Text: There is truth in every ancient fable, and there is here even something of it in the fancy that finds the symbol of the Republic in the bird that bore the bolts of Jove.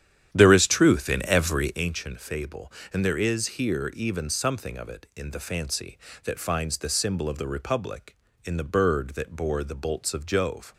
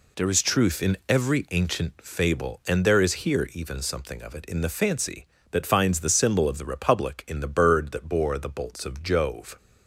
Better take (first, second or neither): second